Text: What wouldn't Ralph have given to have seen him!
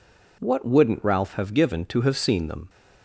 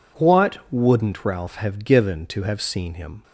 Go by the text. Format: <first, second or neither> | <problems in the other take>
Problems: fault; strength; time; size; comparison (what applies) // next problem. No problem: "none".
second | says "them" for "him"; at 2.4 s